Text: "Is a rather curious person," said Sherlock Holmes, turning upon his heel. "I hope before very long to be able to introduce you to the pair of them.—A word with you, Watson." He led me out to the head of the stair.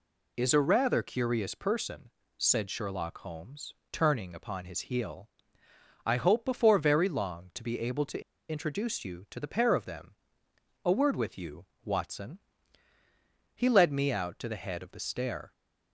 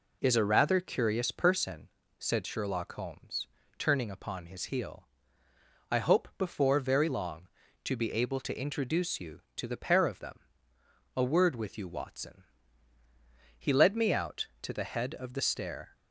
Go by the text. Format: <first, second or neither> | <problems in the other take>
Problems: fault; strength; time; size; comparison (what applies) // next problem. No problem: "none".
second | pauses between "to" and "introduce"; slight; at 8.2 s; 0.29 s long